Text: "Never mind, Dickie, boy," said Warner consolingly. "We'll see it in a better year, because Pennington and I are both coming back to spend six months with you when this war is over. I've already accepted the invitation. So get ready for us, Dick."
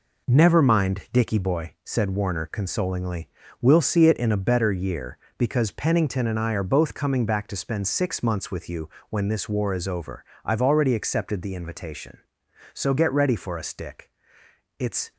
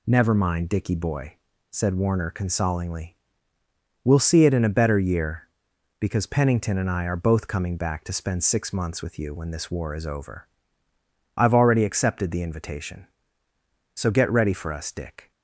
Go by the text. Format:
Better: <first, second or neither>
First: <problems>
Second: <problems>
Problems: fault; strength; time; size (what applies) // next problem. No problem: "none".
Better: second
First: pauses between "you" and "when"; slight; at 8.8 s; 0.20 s long // goes on to say "It's"; slight; from 14.8 s on; 0.32 s long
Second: none